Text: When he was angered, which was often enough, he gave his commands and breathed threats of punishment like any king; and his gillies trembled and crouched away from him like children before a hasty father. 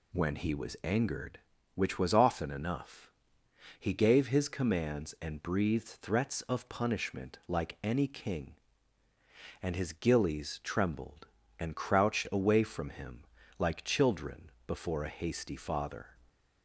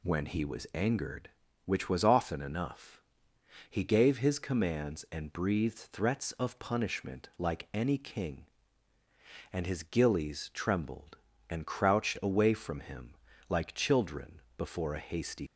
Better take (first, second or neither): first